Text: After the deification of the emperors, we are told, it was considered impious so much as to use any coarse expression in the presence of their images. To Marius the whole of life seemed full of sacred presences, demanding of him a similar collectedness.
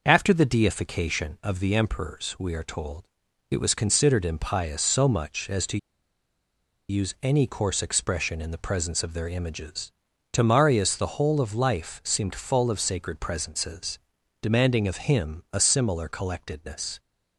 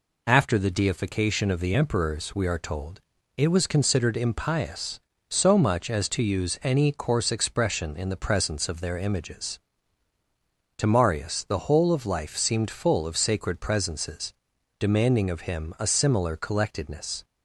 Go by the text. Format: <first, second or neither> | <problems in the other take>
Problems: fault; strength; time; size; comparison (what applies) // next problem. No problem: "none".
second | pauses between "to" and "use"; at 5.7 s; 1.1 s long